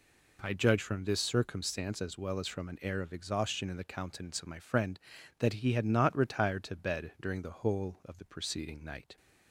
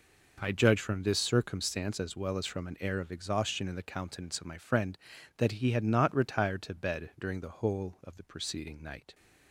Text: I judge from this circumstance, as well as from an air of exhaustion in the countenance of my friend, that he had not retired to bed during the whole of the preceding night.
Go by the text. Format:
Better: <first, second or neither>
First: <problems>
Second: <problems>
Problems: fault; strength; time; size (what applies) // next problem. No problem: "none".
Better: first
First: none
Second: gets quieter; strong; throughout; 12.5 dB